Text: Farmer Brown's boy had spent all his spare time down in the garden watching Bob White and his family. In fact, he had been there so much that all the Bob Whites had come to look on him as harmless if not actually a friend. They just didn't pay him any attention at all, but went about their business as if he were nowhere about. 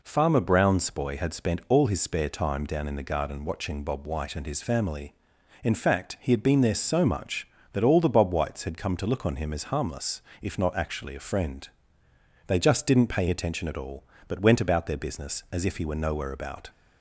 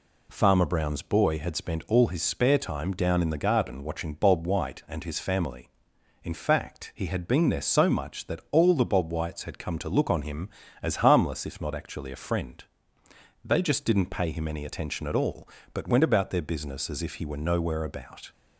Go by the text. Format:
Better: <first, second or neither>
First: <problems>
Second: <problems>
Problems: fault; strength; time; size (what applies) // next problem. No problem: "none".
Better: second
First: pauses between "harmless" and "if"; slight; at 10.2 s; 0.20 s long // skips "him any"; at 13.2 s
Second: none